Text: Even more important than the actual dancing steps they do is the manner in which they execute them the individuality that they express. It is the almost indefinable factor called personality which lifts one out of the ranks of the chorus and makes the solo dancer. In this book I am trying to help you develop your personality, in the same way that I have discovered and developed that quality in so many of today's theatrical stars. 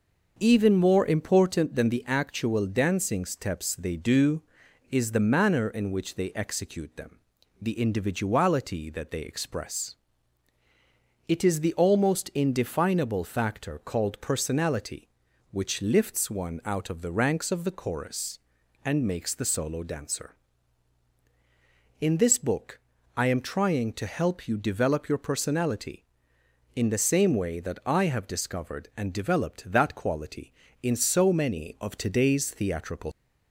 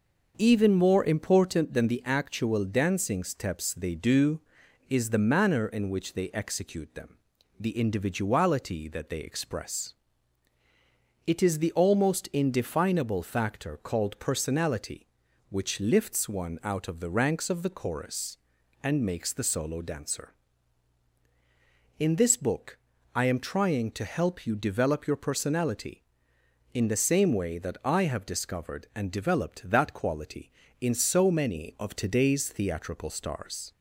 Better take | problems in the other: second | starts louder than the rest; noticeable; until 1.4 s; 6 dB; noticeable in the second // pauses between "them" and "the"; at 7.1 s; 0.42 s long; also in the second // pauses between "book" and "I"; at 22.7 s; 0.38 s long; also in the second // stops before "stars"; at 33.1 s

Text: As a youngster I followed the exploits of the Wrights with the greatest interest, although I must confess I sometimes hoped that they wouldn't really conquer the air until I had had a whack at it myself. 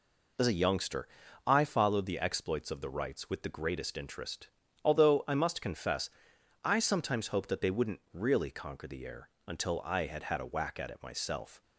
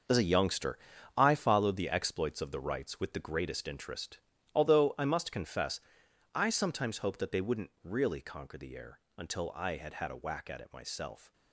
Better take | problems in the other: first | gets quieter; strong; throughout; 10.5 dB // pauses between "youngster" and "I"; at 0.7 s; 0.40 s long; also in the first // pauses between "confess" and "I"; noticeable; at 5.8 s; 0.54 s long; noticeable in the first // pauses between "air" and "until"; slight; at 8.9 s; 0.18 s long; slight in the first

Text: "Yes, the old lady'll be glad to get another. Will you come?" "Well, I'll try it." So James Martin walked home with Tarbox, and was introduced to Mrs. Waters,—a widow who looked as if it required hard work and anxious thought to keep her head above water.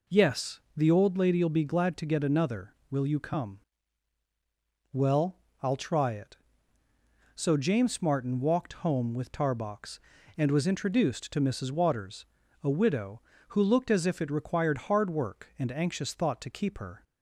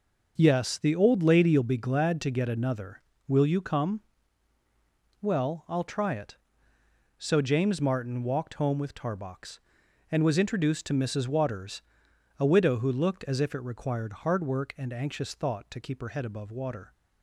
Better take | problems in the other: second | stops before "head above water"; at 17.0 s

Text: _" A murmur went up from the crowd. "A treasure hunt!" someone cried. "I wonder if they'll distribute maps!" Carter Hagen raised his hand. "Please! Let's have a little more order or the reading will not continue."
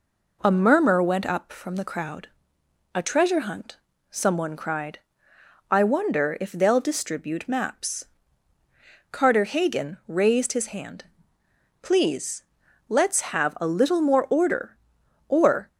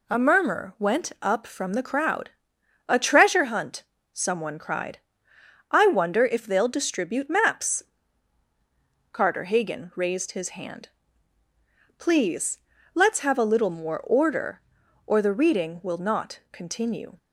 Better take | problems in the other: second | stops before "the reading will not continue"; at 15.6 s

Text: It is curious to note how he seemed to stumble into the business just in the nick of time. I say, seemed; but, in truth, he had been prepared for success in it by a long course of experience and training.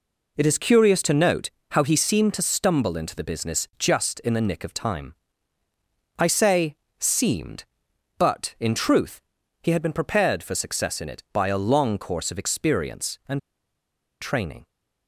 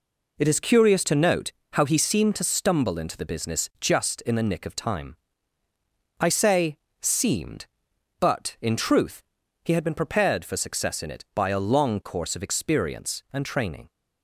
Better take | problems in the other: second | pauses between "note" and "how"; slight; at 1.5 s; 0.20 s long; slight in the second // pauses between "and" and "training"; noticeable; at 13.3 s; 0.81 s long

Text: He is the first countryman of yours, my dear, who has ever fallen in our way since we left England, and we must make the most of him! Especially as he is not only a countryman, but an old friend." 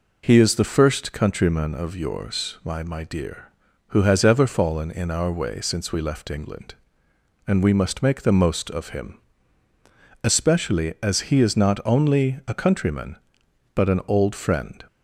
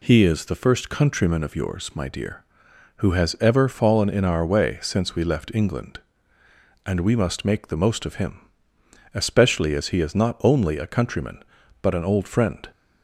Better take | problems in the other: second | says "my" twice; at 2.8 s

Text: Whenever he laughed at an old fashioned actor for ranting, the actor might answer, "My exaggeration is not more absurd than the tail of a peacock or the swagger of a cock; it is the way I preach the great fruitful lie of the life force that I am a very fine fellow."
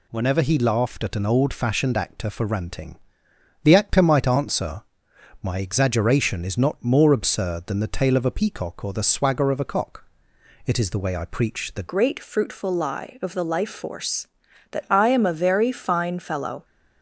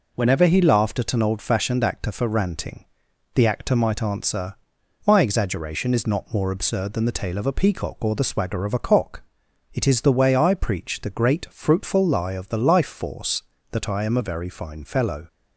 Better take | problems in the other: second | changes voice at "great"; from 11.8 s on; 4.8 s long

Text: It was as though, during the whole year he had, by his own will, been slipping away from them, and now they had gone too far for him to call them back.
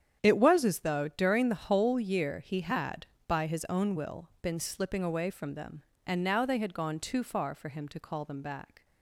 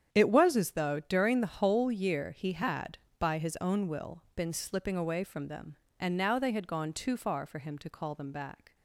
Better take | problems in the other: neither | starts louder than the rest; strong; the same in both

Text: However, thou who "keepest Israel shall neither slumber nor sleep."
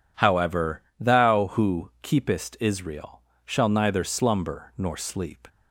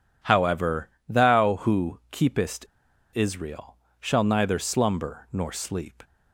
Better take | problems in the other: first | pauses between "keepest" and "Israel"; noticeable; at 2.6 s; 0.50 s long // pauses between "Israel" and "shall"; slight; at 3.7 s; 0.24 s long; slight in the first

